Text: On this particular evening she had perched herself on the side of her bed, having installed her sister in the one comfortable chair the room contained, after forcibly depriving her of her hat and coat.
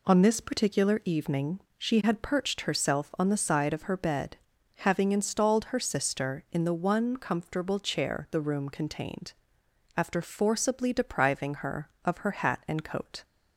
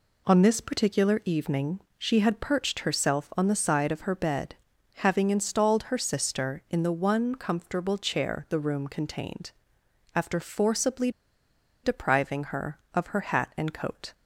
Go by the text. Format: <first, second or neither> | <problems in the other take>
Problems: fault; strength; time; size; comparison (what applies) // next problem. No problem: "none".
first | pauses between "evening" and "she"; slight; at 1.7 s; 0.18 s long; slight in the first // pauses between "forcibly" and "depriving"; noticeable; at 11.0 s; 0.73 s long